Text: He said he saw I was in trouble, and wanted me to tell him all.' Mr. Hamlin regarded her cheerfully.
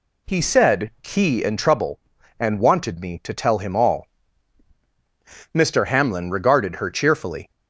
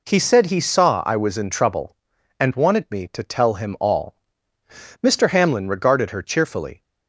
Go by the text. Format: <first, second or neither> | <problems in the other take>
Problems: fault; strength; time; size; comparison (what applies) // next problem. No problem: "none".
second | skips "saw I was"; at 1.4 s